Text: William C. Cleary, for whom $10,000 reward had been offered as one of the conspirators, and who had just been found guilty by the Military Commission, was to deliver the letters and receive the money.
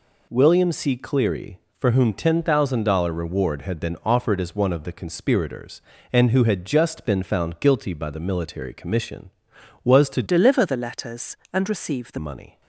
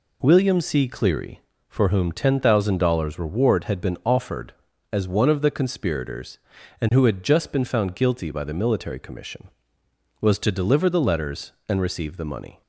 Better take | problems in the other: second | changes voice from "deliver" to "the"; from 10.2 to 12.1 s; 1.9 s long

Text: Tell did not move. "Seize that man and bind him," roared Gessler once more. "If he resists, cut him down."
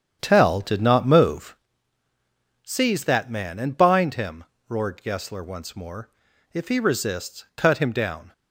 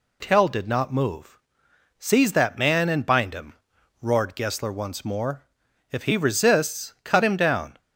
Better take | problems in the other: second | starts louder than the rest; strong; until 1.7 s; 9 dB

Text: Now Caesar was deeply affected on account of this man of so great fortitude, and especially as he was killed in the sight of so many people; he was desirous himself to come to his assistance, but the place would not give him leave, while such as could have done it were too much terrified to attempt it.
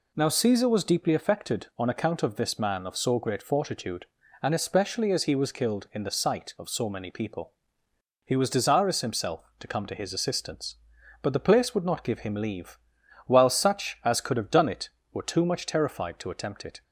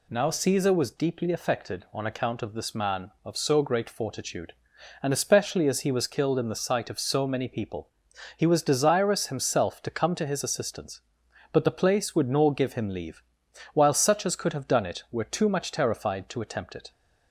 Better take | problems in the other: first | says "nor" for "not"; at 12.2 s

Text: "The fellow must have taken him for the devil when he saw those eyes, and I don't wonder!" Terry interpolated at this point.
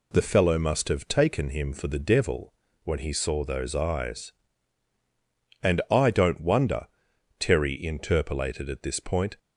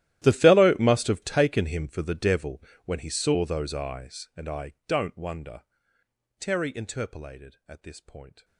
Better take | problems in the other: first | gets quieter; strong; throughout; 22 dB // pauses between "devil" and "when"; slight; at 2.6 s; 0.22 s long; slight in the first

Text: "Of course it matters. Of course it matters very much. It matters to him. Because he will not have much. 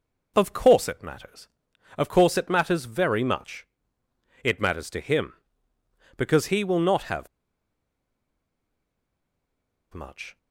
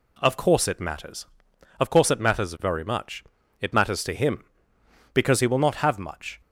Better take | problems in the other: second | pauses between "have" and "much"; strong; at 7.2 s; 2.6 s long

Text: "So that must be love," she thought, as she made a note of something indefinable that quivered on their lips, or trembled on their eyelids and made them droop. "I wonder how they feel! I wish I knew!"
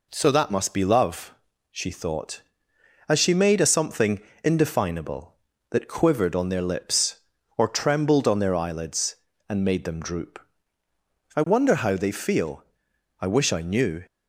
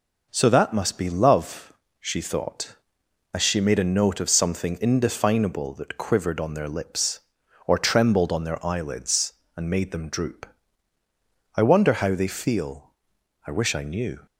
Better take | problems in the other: second | skips "note of"; at 3.6 s // pauses between "something" and "indefinable"; slight; at 4.1 s; 0.24 s long

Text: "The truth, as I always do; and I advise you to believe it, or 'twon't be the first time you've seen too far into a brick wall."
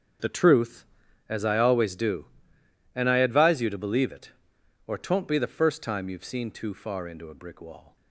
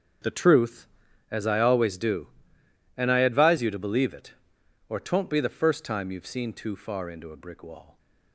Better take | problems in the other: neither | starts louder than the rest; strong; the same in both

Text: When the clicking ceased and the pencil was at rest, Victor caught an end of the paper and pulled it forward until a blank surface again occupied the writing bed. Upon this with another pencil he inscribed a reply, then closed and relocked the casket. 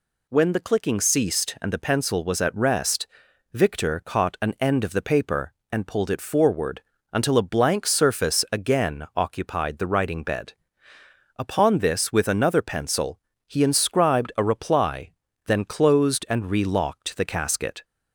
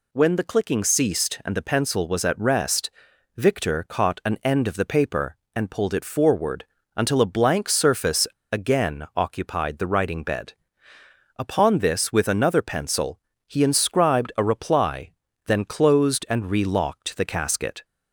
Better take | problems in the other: first | pauses between "forward" and "until"; slight; at 6.6 s; 0.30 s long; slight in the first // pauses between "surface" and "again"; slight; at 8.2 s; 0.24 s long // pauses between "pencil" and "he"; slight; at 13.1 s; 0.28 s long; slight in the first

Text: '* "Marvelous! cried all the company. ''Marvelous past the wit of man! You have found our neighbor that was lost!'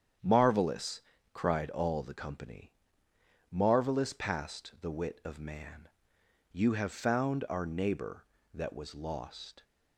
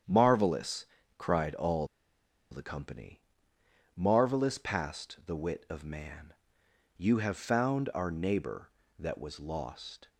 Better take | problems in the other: first | starts louder than the rest; strong; until 1.3 s; 9 dB; strong in the first // pauses between "all" and "the"; noticeable; at 1.8 s; 0.64 s long

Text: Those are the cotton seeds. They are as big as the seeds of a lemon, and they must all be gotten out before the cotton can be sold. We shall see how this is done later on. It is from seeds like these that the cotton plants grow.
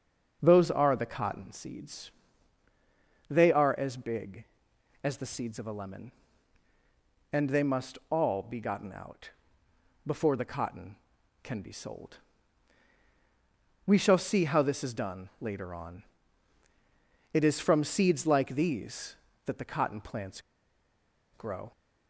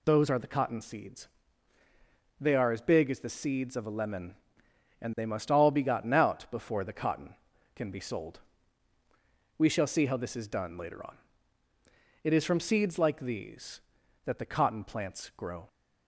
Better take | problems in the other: second | starts louder than the rest; until 1.4 s; 6.5 dB // pauses between "out" and "before"; noticeable; at 9.2 s; 0.76 s long // pauses between "plants" and "grow"; noticeable; at 20.3 s; 0.93 s long

